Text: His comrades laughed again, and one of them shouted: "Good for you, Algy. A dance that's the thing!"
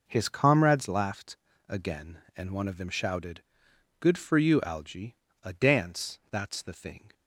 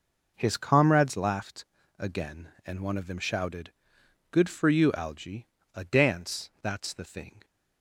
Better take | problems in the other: neither | pauses between "laughed" and "again"; slight; the same in both

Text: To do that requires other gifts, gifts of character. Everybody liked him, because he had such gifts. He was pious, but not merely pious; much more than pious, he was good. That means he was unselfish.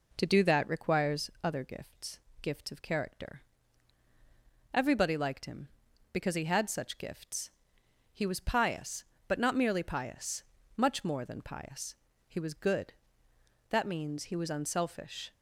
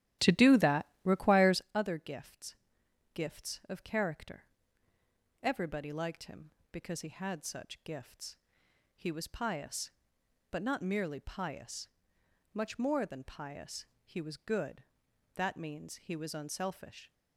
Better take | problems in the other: first | starts louder than the rest; strong; until 1.7 s; 13 dB // pauses between "that" and "requires"; slight; at 0.8 s; 0.20 s long

